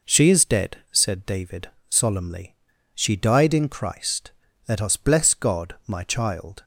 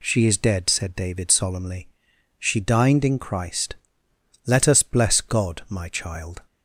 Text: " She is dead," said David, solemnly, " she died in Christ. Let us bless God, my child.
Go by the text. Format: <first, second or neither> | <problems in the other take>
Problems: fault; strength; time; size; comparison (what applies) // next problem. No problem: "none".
first | says "dined" for "died"; at 2.5 s